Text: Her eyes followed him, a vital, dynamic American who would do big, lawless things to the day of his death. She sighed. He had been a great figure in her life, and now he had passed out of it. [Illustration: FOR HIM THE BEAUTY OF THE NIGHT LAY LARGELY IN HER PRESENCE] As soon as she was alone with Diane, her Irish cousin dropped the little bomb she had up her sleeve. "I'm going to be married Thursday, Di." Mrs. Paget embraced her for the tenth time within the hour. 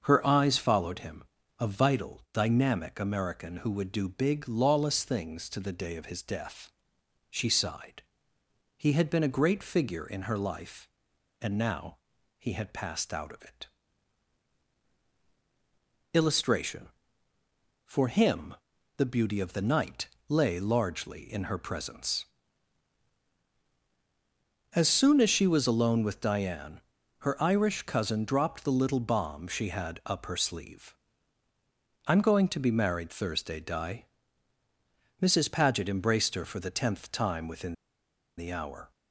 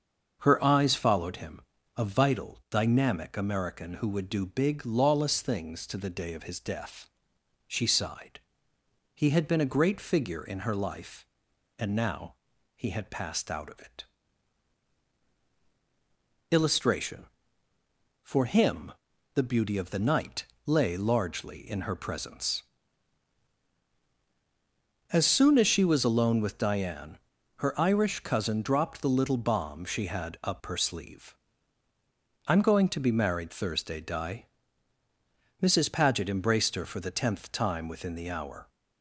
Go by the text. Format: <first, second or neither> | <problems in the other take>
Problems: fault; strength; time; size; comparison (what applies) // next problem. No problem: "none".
second | starts louder than the rest; until 1.0 s; 7 dB; also in the second // pauses between "now" and "he"; at 11.9 s; 0.42 s long; also in the second // pauses between "HIM" and "THE"; at 18.5 s; 0.42 s long; also in the second // pauses between "NIGHT" and "LAY"; slight; at 20.0 s; 0.20 s long; slight in the second // pauses between "within" and "the"; noticeable; at 37.7 s; 0.63 s long